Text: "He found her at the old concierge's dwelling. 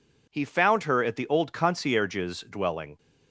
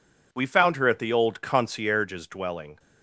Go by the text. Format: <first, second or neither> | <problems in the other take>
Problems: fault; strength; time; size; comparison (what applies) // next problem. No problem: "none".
first | says "We" for "He"; at 0.3 s